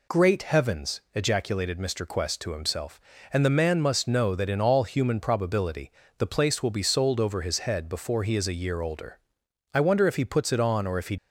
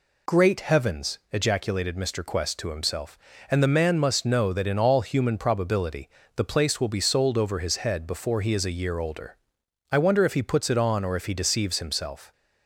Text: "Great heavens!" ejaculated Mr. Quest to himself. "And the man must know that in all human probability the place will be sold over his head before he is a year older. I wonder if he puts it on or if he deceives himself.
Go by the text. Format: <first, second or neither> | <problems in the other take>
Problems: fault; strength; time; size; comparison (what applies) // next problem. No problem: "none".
second | pauses between "probability" and "the"; slight; at 5.9 s; 0.28 s long; slight in the second // stops before "deceives himself"; at 11.1 s